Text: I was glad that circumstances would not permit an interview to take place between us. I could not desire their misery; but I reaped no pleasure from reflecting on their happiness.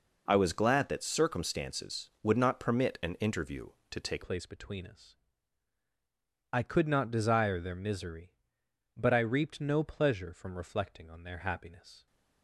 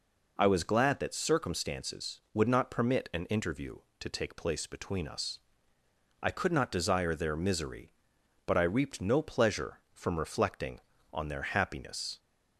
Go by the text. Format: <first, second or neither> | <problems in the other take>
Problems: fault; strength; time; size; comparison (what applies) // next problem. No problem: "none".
second | changes voice at "place"; from 4.2 s on; 7.8 s long